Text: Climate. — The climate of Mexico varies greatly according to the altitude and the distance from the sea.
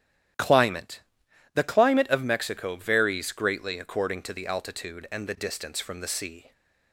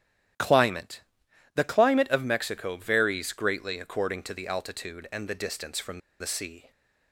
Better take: first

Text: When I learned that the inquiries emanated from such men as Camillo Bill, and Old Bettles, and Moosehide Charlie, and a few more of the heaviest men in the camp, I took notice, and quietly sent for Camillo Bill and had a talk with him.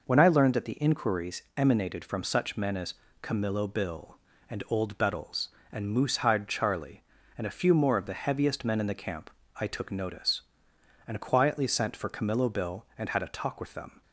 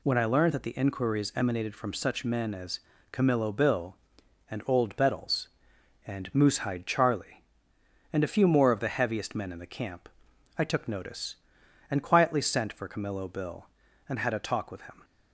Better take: second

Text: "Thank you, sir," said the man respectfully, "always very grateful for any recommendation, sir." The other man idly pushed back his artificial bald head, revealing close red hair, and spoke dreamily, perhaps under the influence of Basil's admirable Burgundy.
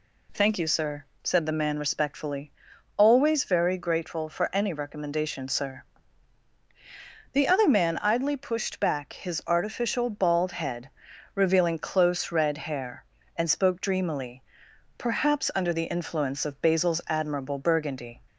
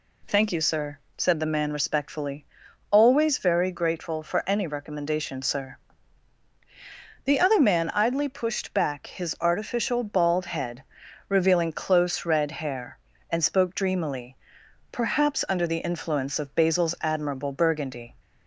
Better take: neither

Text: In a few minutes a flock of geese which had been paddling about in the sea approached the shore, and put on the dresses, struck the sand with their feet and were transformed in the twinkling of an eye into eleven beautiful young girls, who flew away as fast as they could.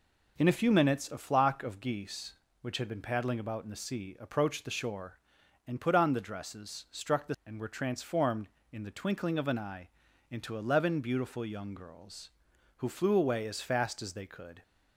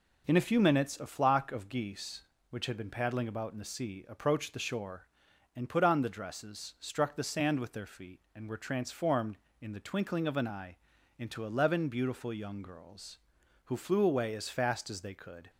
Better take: second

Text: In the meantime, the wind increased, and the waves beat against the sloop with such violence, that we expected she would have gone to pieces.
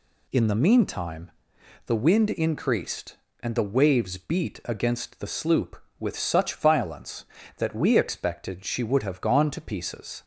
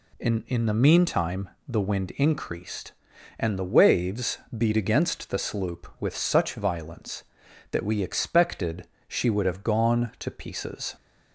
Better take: first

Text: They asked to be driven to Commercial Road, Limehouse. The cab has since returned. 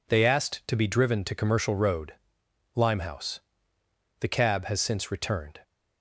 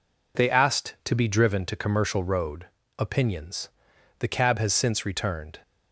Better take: first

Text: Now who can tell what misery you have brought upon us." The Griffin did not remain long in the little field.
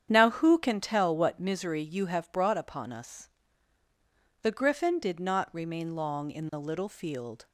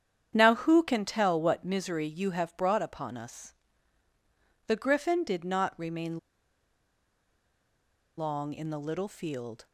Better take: first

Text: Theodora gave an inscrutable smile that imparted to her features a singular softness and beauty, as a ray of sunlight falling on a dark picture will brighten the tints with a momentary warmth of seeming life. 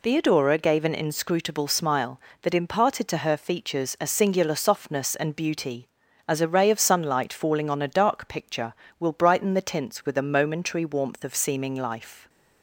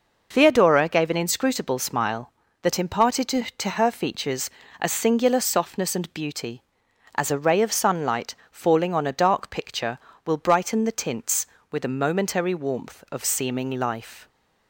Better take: first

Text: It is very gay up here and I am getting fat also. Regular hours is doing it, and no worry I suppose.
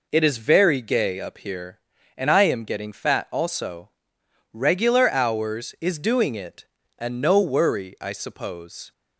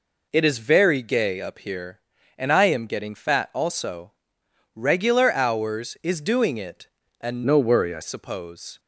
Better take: first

